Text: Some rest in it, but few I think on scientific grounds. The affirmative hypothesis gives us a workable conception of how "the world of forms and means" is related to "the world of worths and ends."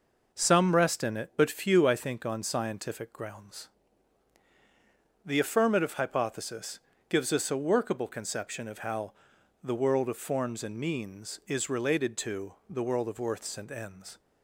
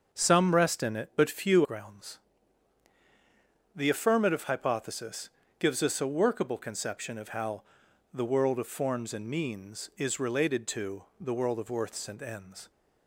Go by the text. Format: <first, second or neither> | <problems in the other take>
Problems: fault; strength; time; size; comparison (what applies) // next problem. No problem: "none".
first | starts louder than the rest; until 1.2 s; 7 dB // skips "I think on scientific"; at 1.6 s // pauses between "hypothesis" and "gives"; slight; at 5.2 s; 0.30 s long; slight in the first // pauses between "how" and "the"; noticeable; at 7.6 s; 0.50 s long; noticeable in the first // pauses between "to" and "the"; slight; at 11.0 s; 0.16 s long; slight in the first